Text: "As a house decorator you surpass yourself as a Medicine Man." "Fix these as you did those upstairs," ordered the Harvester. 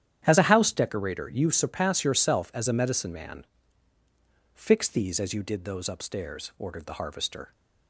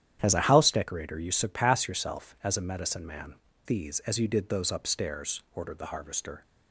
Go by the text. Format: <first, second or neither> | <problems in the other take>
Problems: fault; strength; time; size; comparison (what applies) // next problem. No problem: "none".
first | starts louder than the rest; strong; until 1.2 s; 10.5 dB; strong in the first // skips "Fix"; at 3.5 s